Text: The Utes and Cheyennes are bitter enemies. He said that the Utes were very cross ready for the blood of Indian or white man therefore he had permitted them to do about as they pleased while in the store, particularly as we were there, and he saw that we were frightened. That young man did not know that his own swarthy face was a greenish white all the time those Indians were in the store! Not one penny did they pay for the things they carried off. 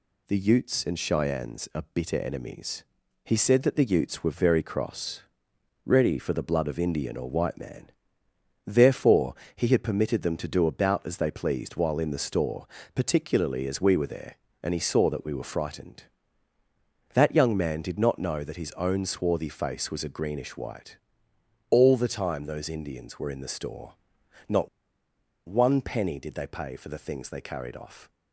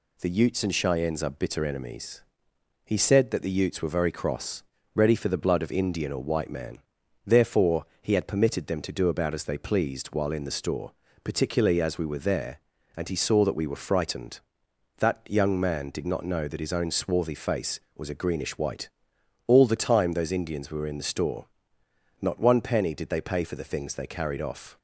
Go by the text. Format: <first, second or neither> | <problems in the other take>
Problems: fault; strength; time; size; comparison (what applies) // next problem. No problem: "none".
second | pauses between "cross" and "ready"; noticeable; at 5.2 s; 0.66 s long; slight in the second // pauses between "man" and "therefore"; noticeable; at 7.9 s; 0.74 s long; also in the second // pauses between "therefore" and "he"; slight; at 9.3 s; 0.20 s long; slight in the second // pauses between "white" and "all"; noticeable; at 20.9 s; 0.72 s long; noticeable in the second // pauses between "Not" and "one"; noticeable; at 24.6 s; 0.80 s long